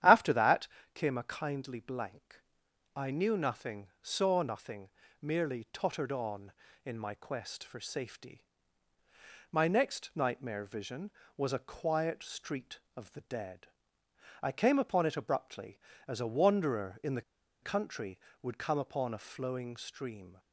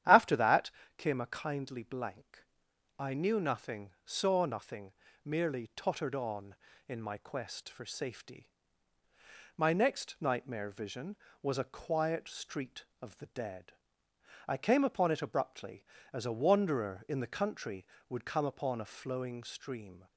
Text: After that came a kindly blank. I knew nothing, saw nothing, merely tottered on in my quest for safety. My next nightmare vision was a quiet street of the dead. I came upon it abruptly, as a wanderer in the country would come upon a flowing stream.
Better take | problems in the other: second | starts louder than the rest; strong; until 1.3 s; 10.5 dB; strong in the second // pauses between "that" and "came"; slight; at 0.6 s; 0.28 s long; slight in the second // pauses between "the" and "country"; at 17.2 s; 0.41 s long

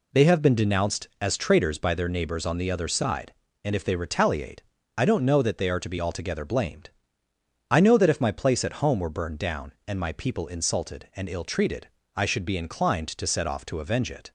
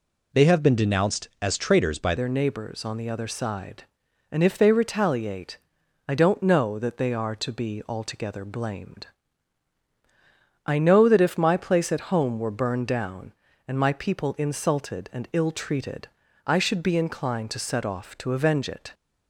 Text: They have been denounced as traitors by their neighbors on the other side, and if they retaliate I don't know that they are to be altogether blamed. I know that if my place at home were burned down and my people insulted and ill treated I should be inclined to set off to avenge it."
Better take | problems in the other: first | changes voice at "their"; from 2.1 s on; 16.8 s long // pauses between "retaliate" and "I"; noticeable; at 5.5 s; 0.50 s long; slight in the first // pauses between "treated" and "I"; slight; at 16.0 s; 0.36 s long; slight in the first

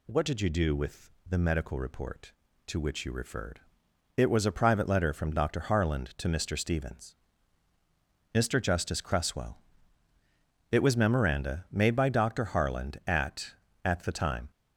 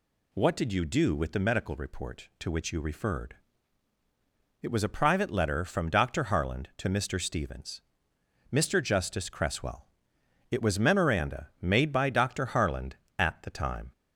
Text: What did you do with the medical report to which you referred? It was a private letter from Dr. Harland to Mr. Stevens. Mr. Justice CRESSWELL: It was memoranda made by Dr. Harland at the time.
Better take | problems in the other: second | pauses between "with" and "the"; slight; at 1.0 s; 0.20 s long // says "at" twice; at 13.8 s

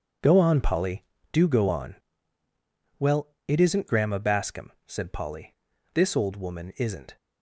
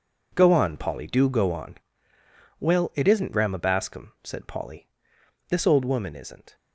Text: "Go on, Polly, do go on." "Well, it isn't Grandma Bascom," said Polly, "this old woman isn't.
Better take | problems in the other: neither | none

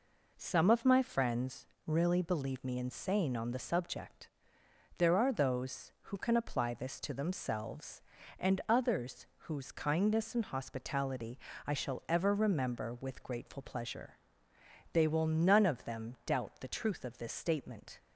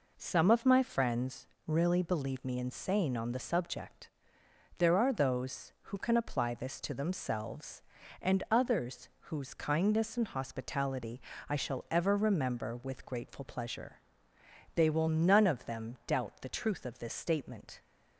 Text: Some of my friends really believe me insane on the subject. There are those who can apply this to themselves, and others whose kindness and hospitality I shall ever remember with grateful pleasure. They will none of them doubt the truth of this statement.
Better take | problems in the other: neither | pauses between "friends" and "really"; slight; the same in both // pauses between "others" and "whose"; slight; the same in both // pauses between "hospitality" and "I"; slight; the same in both

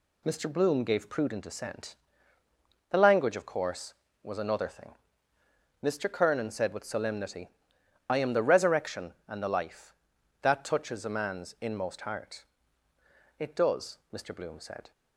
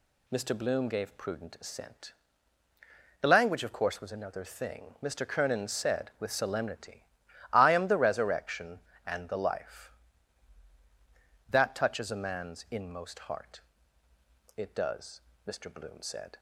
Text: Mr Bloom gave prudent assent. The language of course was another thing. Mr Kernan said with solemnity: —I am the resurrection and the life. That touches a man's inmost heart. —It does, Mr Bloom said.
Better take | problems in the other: neither | none

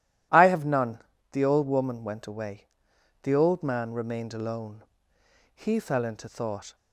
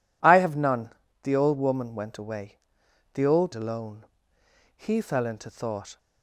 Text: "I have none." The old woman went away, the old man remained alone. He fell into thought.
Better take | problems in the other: first | skips "man remained"; at 3.5 s

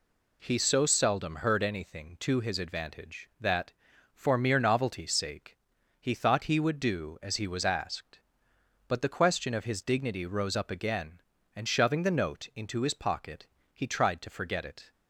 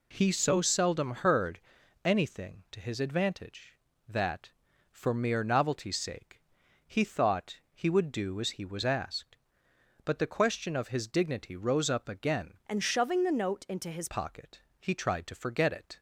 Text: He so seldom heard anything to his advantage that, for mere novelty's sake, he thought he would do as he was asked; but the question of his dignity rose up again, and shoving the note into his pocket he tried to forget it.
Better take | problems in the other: first | pauses between "heard" and "anything"; at 1.6 s; 0.42 s long // changes voice from "and" to "his"; from 12.6 to 14.0 s; 1.4 s long // pauses between "pocket" and "he"; slight; at 14.6 s; 0.18 s long; slight in the first

